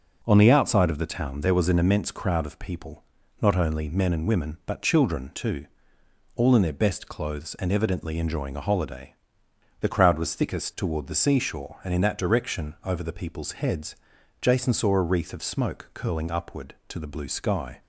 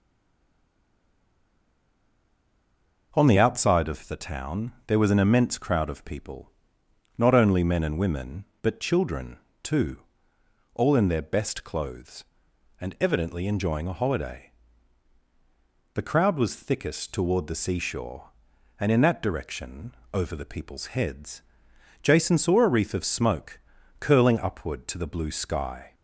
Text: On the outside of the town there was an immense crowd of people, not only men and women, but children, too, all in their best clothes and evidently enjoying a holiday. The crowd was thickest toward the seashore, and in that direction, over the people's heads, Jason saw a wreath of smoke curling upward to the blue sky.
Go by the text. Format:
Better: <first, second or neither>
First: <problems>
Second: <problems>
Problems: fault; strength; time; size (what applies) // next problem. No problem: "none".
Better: first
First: none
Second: stays silent before the first word; strong; until 3.1 s; 3.1 s long // pauses between "smoke" and "curling"; at 23.5 s; 0.42 s long